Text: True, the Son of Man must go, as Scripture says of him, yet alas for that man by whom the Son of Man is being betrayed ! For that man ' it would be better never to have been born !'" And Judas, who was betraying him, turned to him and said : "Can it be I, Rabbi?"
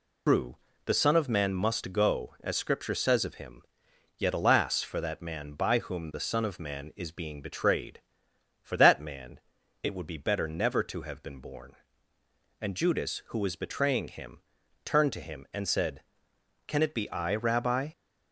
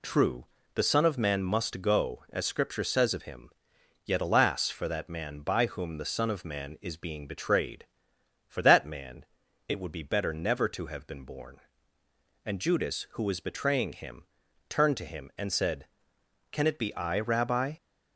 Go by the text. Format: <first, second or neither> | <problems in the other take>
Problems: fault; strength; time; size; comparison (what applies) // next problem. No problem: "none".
second | loses the start of "True"; at 0.2 s; 140 ms